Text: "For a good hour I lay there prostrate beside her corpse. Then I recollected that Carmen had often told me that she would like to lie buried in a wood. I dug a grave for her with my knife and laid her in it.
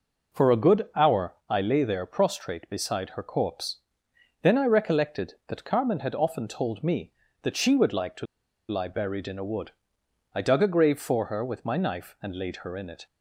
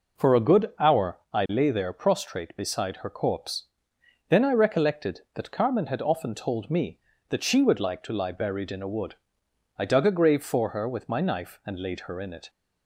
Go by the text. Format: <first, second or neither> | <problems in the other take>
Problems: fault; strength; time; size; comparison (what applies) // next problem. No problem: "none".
second | pauses between "to" and "lie"; at 8.2 s; 0.44 s long